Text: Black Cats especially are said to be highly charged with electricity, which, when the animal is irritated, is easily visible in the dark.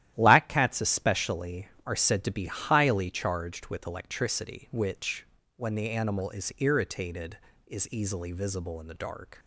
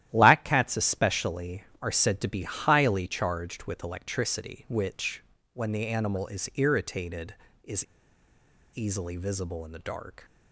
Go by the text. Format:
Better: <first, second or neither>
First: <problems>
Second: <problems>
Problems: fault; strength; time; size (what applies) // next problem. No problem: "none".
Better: first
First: starts louder than the rest; strong; until 1.1 s; 13 dB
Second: starts louder than the rest; strong; until 1.1 s; 13 dB // pauses between "is" and "easily"; noticeable; at 7.8 s; 0.89 s long